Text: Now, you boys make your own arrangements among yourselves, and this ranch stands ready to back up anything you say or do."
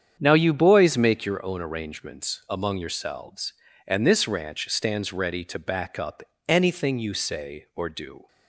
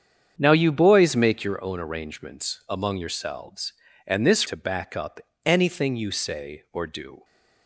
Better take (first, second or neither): first